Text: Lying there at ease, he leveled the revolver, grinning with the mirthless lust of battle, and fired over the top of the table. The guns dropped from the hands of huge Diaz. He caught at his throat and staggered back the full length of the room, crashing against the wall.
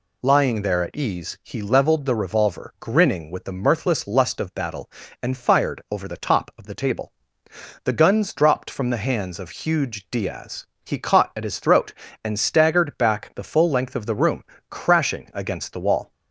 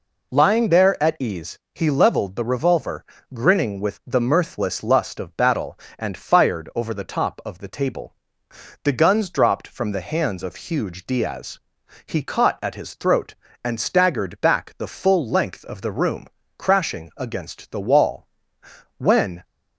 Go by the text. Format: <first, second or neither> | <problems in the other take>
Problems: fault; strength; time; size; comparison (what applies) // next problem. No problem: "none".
first | goes on to say "When"; slight; from 18.9 s on; 0.48 s long